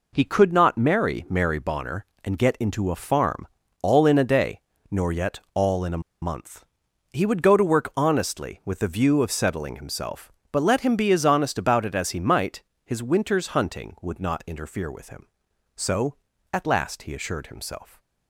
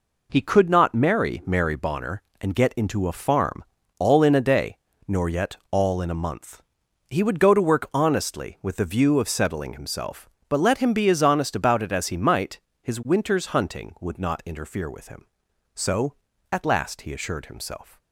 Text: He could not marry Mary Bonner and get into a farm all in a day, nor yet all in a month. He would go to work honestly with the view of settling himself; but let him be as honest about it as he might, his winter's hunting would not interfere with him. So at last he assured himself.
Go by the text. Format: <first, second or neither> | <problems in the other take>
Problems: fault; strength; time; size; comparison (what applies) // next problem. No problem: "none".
second | pauses between "farm" and "all"; slight; at 3.4 s; 0.34 s long; slight in the second // pauses between "a" and "month"; slight; at 6.0 s; 0.21 s long